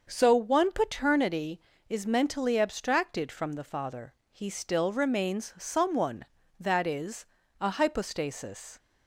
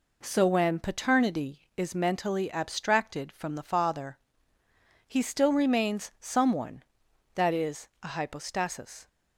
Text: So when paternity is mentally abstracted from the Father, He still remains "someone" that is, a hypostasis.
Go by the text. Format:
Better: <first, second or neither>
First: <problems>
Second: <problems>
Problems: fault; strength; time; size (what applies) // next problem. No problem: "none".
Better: second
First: starts louder than the rest; until 1.1 s; 6.5 dB // says "one" for "when"; at 0.3 s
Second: none